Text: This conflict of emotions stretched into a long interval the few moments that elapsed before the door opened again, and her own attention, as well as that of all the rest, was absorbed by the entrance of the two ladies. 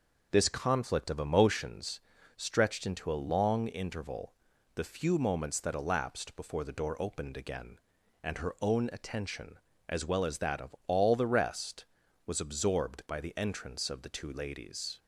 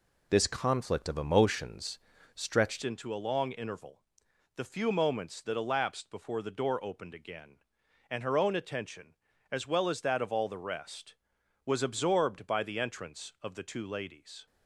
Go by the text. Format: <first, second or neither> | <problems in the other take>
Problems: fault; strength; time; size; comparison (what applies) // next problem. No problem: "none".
first | pauses between "emotions" and "stretched"; slight; at 1.9 s; 0.36 s long; slight in the first // changes voice at "into"; from 2.8 s on; 11.6 s long // pauses between "interval" and "the"; noticeable; at 4.0 s; 0.52 s long; also in the first